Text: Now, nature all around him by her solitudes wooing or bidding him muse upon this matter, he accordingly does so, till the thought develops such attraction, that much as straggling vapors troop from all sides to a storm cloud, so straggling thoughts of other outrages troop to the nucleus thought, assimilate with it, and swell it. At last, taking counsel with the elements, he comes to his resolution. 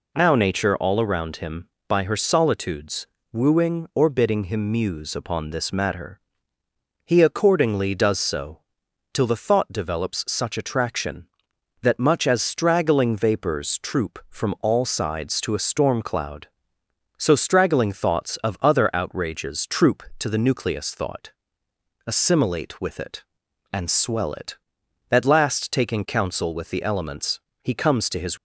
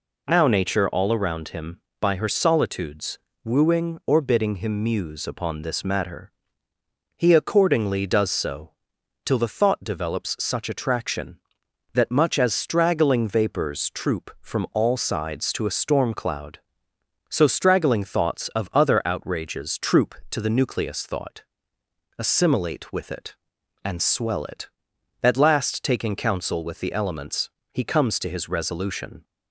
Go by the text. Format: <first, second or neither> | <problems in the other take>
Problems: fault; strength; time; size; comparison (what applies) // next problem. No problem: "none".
second | pauses between "solitudes" and "wooing"; slight; at 3.0 s; 0.26 s long; slight in the second // stops before "resolution"; at 28.3 s